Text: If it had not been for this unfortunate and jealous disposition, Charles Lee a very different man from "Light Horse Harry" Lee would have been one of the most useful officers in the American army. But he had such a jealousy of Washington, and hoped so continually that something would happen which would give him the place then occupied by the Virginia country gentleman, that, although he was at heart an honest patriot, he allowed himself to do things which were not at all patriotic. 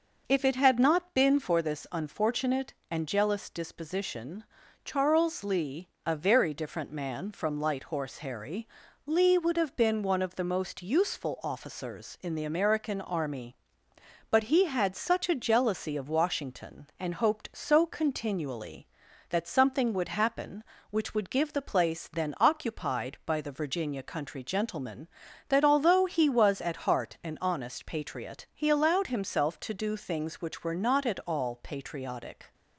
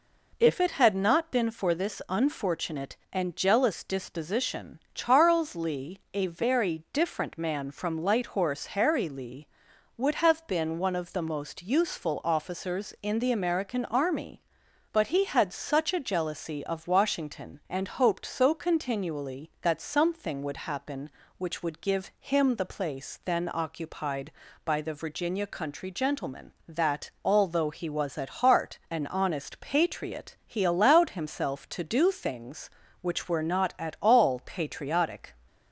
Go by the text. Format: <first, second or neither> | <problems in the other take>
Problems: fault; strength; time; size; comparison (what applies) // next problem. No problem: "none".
second | pauses between "Lee" and "a"; slight; at 5.8 s; 0.16 s long // pauses between "Harry" and "Lee"; at 8.6 s; 0.38 s long // skips "him"; at 21.5 s